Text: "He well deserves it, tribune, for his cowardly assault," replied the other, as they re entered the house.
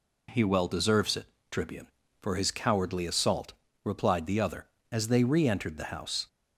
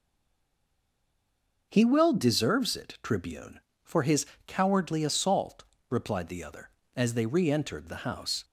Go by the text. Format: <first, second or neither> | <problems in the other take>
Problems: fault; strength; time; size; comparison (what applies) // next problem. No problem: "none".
first | stays silent before the first word; noticeable; until 1.7 s; 1.7 s long // starts louder than the rest; until 2.7 s; 6 dB // pauses between "his" and "cowardly"; slight; at 4.2 s; 0.22 s long